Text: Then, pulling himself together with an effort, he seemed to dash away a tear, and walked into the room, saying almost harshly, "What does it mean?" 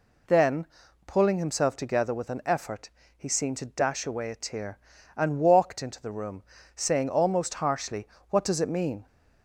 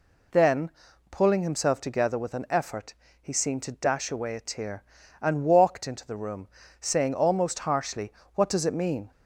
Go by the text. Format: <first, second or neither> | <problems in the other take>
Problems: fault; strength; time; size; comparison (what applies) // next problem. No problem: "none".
neither | none